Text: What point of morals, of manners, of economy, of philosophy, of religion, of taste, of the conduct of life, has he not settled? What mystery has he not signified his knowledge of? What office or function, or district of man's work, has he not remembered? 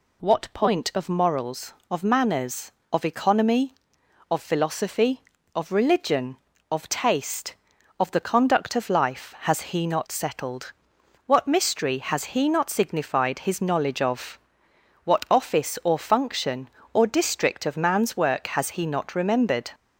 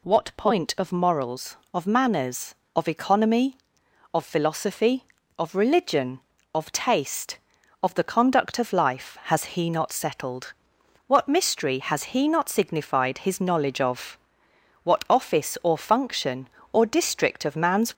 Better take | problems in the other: first | stops before "work has he not remembered"; at 17.9 s

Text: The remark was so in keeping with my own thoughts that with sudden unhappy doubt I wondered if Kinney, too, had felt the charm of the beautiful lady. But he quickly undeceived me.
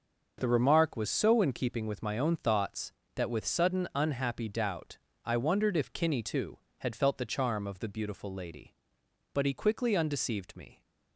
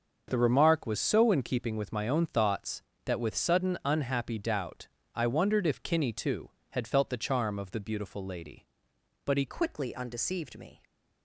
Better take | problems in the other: first | starts louder than the rest; noticeable; until 1.2 s; 6 dB // pauses between "doubt" and "I"; slight; at 4.8 s; 0.28 s long; slight in the first // changes voice at "quickly"; from 9.4 s on; 1.4 s long

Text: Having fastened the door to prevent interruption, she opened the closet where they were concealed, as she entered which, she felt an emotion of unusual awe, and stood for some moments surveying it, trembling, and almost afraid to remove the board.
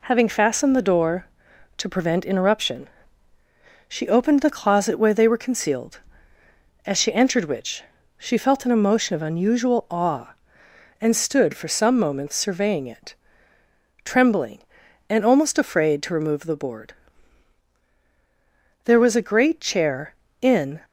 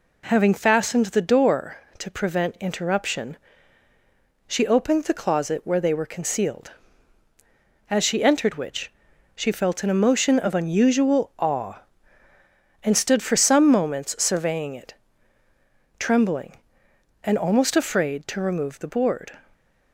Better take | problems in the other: second | goes on to say "There was a great chair in"; strong; from 18.8 s on; 1.9 s long

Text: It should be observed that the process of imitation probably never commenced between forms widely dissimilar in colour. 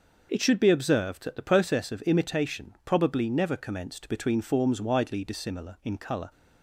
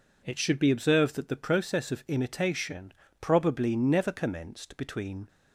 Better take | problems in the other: first | stops before "forms widely dissimilar in colour"; at 5.2 s

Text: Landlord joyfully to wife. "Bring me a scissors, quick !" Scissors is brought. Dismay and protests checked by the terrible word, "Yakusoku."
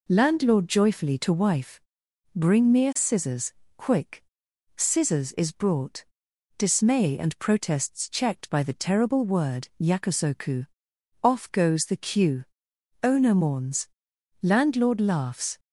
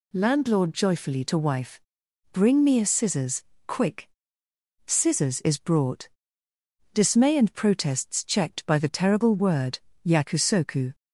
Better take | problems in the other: second | goes on to say "Off goes the queue Owner mourns Landlord laughs"; strong; from 11.2 s on; 4.3 s long

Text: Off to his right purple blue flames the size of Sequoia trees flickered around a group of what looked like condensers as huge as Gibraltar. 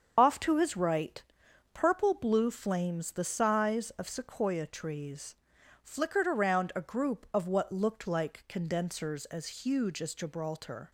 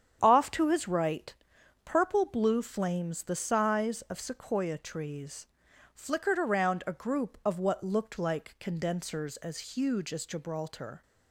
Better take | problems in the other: second | loses the start of "Off"; at 0.1 s; 85 ms // starts louder than the rest; strong; until 1.1 s; 7 dB; strong in the second // pauses between "right" and "purple"; noticeable; at 1.2 s; 0.52 s long; noticeable in the second // pauses between "trees" and "flickered"; noticeable; at 5.3 s; 0.48 s long; noticeable in the second

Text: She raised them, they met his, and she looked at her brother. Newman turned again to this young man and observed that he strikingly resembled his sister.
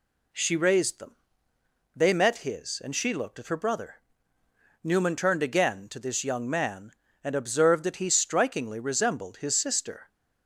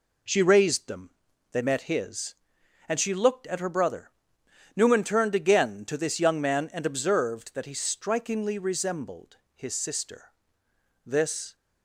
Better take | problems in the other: first | pauses between "resembled" and "his"; slight; at 9.3 s; 0.18 s long // goes on to say "This"; from 11.0 s on; 0.50 s long

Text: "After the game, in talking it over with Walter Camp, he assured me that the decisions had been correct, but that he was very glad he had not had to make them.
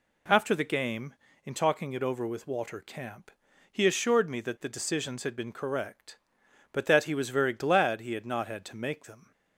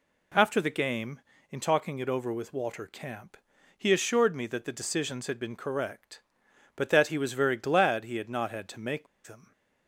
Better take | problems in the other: first | pauses between "make" and "them"; slight; at 9.0 s; 0.19 s long

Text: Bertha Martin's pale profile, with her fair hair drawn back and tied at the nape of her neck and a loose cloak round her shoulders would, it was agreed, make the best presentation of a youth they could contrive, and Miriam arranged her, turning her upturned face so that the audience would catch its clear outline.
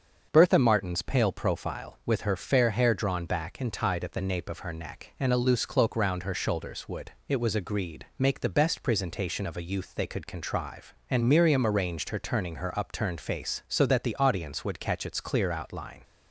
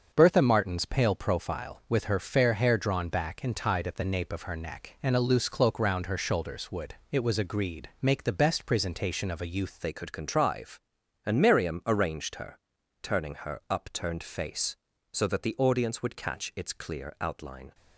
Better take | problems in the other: first | starts louder than the rest; until 1.1 s; 7 dB; also in the first // changes voice at "they"; from 9.8 s on; 7.9 s long

